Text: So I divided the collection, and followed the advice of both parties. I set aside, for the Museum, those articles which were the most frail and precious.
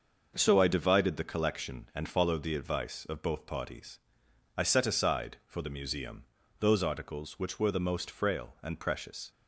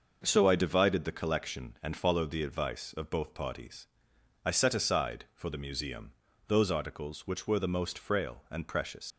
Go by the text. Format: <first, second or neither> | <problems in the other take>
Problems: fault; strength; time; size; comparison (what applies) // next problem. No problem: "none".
first | starts louder than the rest; noticeable; until 1.2 s; 6 dB; noticeable in the first // leaves "precious" unfinished; at 9.1 s; 80 ms